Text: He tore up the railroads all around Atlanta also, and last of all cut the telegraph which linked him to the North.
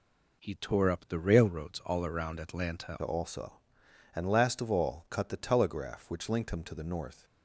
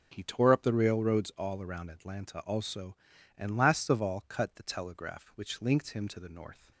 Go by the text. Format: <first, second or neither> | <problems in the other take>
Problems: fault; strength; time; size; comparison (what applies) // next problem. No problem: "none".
second | changes voice at "also"; from 3.0 s on; 4.2 s long